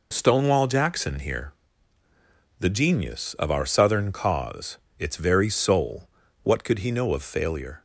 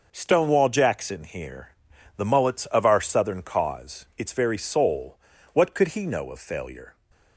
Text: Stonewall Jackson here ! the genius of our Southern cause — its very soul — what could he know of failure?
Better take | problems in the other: first | says "mullets" for "genius"; at 2.2 s

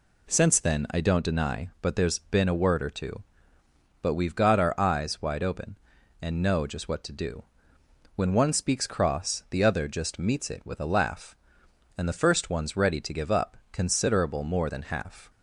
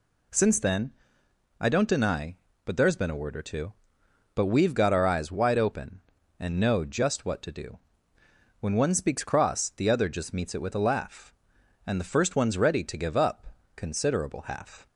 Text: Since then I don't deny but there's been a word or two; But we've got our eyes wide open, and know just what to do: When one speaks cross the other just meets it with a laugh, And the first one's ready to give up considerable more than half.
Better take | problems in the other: first | pauses between "then" and "I"; noticeable; at 0.9 s; 0.68 s long // pauses between "up" and "considerable"; slight; at 13.4 s; 0.28 s long; slight in the first // skips "more than"; at 14.4 s

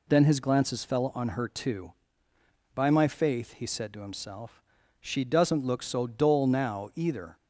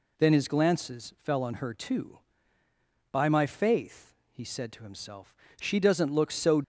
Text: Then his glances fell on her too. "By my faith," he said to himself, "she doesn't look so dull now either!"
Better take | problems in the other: first | stops before "dull now either"; at 6.6 s

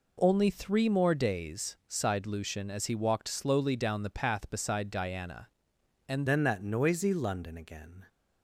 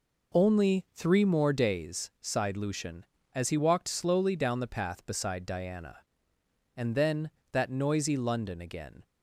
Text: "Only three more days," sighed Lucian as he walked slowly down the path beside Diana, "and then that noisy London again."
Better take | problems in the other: second | changes voice at "then"; from 6.2 s on; 1.8 s long

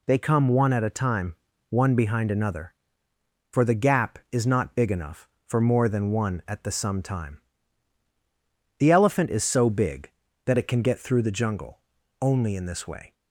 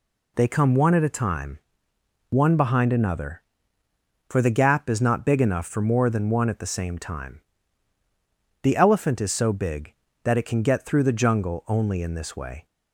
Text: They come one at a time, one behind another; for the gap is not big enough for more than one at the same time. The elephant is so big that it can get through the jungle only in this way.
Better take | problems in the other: second | says "some" for "same"; at 6.7 s // pauses between "jungle" and "only"; at 11.7 s; 0.42 s long

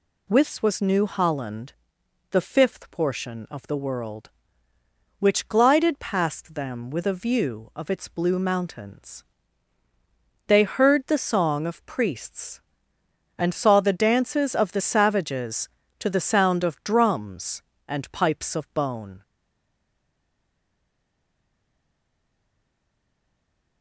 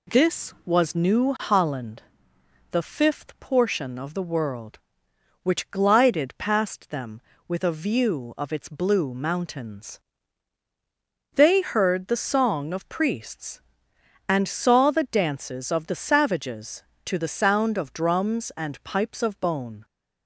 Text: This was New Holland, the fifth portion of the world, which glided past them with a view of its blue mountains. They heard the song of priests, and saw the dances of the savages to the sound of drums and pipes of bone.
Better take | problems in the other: second | stays silent after the last word; strong; from 19.2 s on; 4.6 s long

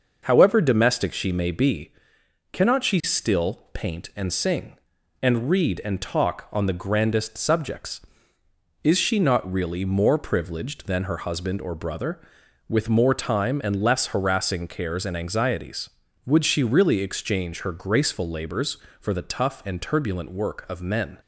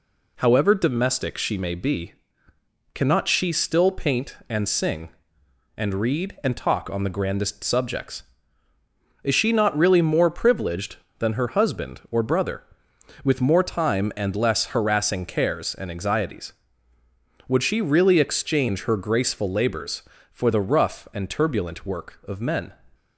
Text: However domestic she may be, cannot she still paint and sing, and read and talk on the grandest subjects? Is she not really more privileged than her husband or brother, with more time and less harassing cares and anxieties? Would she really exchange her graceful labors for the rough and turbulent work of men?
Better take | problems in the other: second | says "tough" for "rough"; at 19.2 s

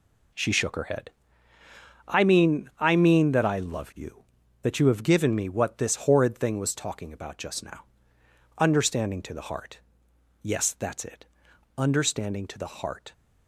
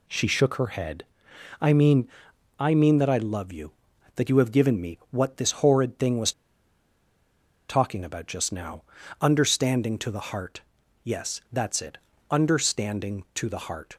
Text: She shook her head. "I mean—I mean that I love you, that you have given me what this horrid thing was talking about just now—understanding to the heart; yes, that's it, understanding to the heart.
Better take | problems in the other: first | pauses between "was" and "talking"; strong; at 6.3 s; 1.3 s long

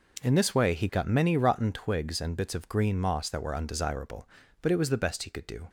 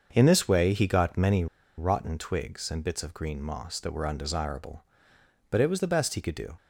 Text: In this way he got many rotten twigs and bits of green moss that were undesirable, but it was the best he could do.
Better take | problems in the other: first | starts louder than the rest; until 1.1 s; 6.5 dB // pauses between "many" and "rotten"; slight; at 1.4 s; 0.32 s long

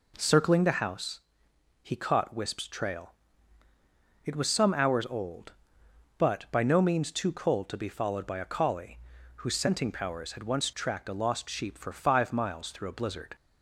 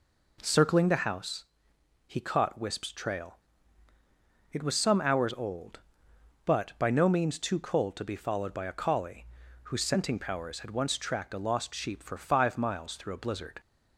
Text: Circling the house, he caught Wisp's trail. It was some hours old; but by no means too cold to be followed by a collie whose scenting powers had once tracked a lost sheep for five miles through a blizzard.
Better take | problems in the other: neither | pauses between "collie" and "whose"; the same in both

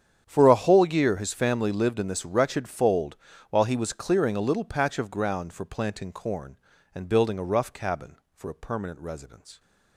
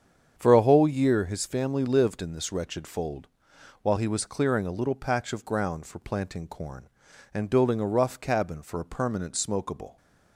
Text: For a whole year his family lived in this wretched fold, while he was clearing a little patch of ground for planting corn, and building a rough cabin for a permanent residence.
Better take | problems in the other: first | starts louder than the rest; strong; until 1.4 s; 8 dB; strong in the first // says "smokable" for "residence"; at 9.3 s

